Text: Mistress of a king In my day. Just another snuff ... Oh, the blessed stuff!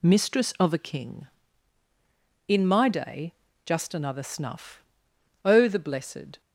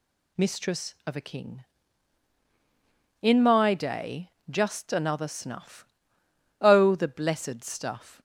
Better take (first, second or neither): second